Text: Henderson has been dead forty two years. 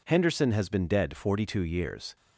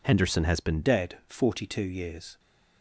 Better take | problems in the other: first | changes voice at "dead"; from 0.8 s on; 1.5 s long

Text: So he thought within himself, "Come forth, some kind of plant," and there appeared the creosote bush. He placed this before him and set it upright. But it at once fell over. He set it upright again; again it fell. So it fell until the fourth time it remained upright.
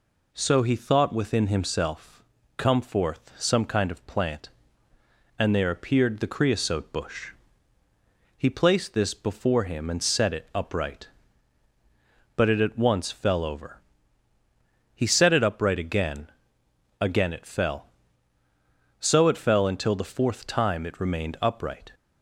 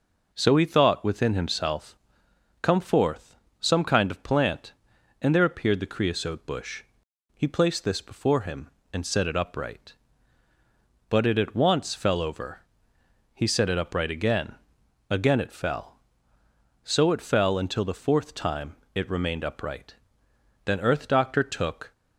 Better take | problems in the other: first | pauses between "time" and "it"; slight; at 18.7 s; 0.18 s long // goes on to say "Then Earth Doctor took"; noticeable; from 20.6 s on; 1.2 s long

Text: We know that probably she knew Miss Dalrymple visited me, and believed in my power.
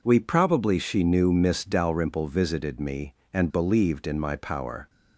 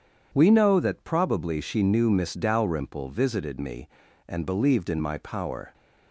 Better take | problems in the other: second | skips "know that"; at 0.1 s

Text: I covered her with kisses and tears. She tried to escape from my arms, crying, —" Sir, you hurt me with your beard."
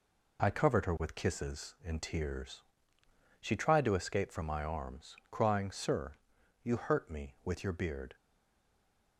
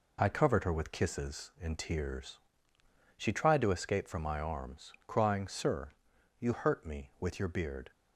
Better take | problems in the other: second | stays silent after the last word; from 8.1 s on; 1.0 s long

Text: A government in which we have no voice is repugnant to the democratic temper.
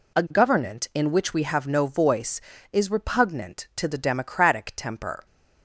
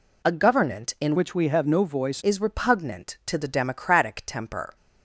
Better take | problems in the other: first | changes voice from "which" to "voice"; from 1.1 to 2.2 s; 1.1 s long

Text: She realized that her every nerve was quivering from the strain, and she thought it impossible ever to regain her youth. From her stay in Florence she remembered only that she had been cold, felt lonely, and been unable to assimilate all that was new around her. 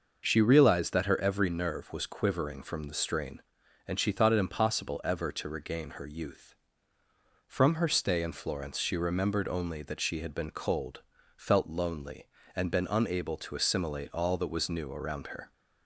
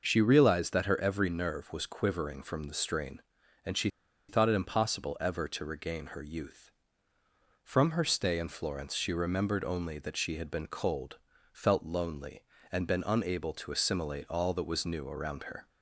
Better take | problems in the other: first | pauses between "she" and "thought"; at 3.8 s; 0.40 s long

